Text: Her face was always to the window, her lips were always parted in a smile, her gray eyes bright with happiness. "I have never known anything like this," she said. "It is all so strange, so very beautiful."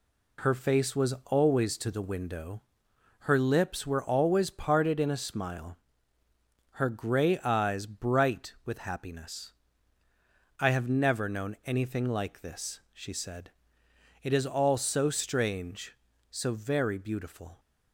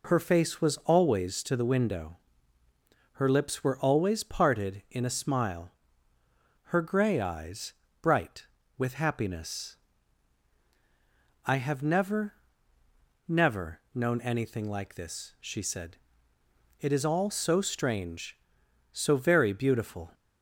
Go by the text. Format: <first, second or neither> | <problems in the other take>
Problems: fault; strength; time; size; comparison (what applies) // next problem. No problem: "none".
first | pauses between "eyes" and "bright"; slight; at 7.7 s; 0.30 s long // says "never" twice; at 13.2 s